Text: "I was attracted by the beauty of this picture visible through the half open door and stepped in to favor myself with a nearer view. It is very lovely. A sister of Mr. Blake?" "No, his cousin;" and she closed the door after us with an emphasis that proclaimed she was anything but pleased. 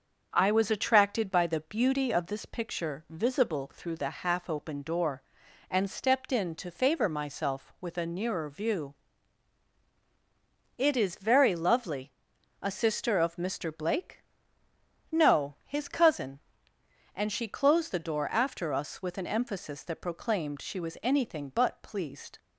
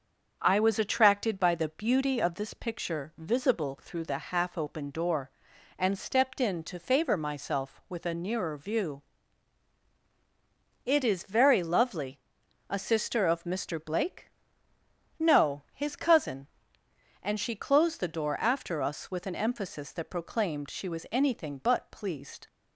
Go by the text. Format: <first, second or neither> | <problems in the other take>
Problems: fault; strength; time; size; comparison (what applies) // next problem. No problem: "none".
neither | starts louder than the rest; the same in both